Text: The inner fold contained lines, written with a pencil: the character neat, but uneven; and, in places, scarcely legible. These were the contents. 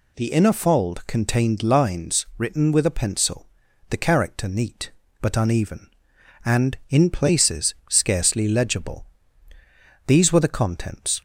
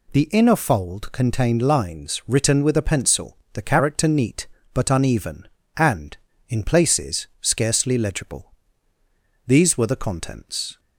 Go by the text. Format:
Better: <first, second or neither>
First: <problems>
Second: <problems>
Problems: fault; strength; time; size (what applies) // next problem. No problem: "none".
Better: neither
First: none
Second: none